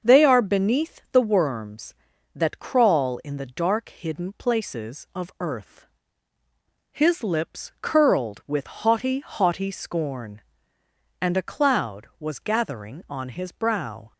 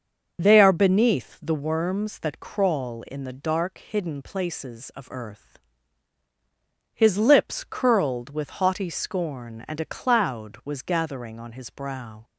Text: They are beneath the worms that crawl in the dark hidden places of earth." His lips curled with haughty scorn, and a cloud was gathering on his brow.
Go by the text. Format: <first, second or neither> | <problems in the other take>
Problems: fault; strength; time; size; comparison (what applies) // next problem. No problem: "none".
second | starts louder than the rest; until 1.1 s; 6.5 dB; also in the second // says "haughty" twice; at 9.2 s